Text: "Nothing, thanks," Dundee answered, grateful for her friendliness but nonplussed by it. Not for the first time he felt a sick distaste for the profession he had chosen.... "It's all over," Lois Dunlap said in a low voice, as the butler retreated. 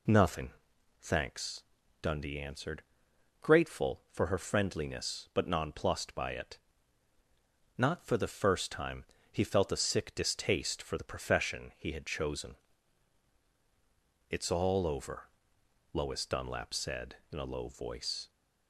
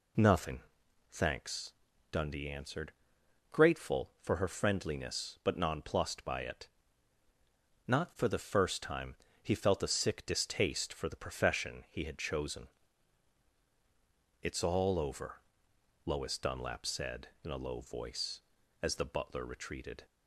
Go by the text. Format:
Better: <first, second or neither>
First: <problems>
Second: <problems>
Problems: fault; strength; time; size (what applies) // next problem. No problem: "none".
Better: second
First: pauses between "time" and "he"; slight; at 9.0 s; 0.28 s long // stops before "as the butler retreated"; at 18.2 s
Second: pauses between "time" and "he"; slight; at 9.1 s; 0.28 s long